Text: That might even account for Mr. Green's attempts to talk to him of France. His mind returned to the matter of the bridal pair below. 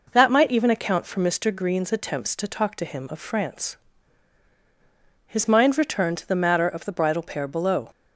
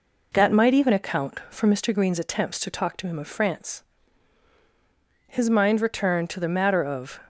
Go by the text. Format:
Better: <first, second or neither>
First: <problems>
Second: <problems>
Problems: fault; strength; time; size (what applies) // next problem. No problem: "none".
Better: first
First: none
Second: stops before "the bridal pair below"; at 7.2 s